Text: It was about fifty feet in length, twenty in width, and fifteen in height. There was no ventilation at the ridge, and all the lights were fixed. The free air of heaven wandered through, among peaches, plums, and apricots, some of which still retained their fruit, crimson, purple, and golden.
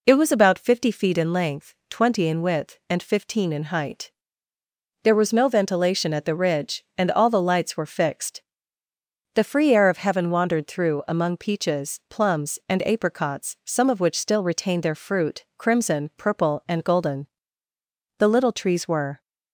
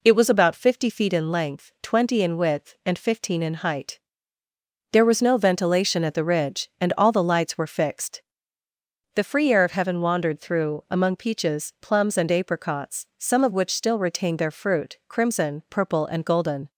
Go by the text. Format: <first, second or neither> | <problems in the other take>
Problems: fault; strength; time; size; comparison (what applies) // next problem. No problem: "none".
second | goes on to say "The little trees were"; noticeable; from 18.1 s on; 1.0 s long